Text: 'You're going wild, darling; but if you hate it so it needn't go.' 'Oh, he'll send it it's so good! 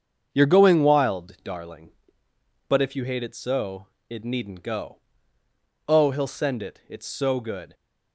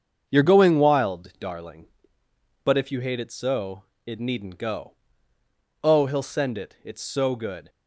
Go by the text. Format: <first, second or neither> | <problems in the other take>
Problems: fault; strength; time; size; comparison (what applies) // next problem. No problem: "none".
neither | starts louder than the rest; the same in both // pauses between "so" and "it"; slight; the same in both